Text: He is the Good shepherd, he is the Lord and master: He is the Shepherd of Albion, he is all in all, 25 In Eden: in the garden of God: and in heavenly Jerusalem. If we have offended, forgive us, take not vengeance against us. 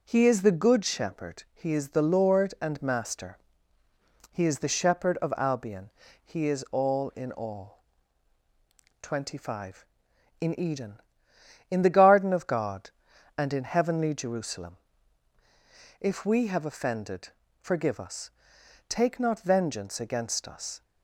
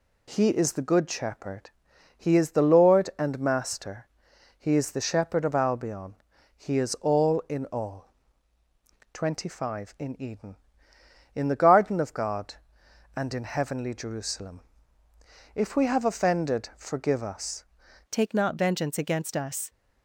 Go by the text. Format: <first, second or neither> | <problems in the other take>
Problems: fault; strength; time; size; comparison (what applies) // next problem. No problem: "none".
first | changes voice at "take"; from 18.0 s on; 1.6 s long